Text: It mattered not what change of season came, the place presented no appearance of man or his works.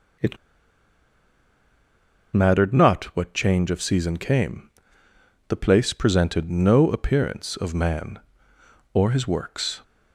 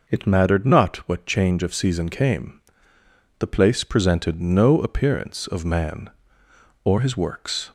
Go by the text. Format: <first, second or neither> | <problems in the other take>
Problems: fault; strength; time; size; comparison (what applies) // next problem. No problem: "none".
second | pauses between "It" and "mattered"; strong; at 0.3 s; 1.9 s long